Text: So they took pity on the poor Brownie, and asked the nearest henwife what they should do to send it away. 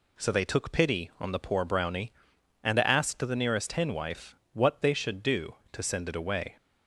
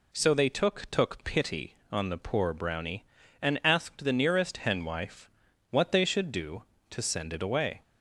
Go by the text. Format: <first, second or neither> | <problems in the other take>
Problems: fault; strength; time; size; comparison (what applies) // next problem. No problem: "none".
first | says "took" twice; at 0.9 s // pauses between "henwife" and "what"; at 5.2 s; 0.40 s long; slight in the first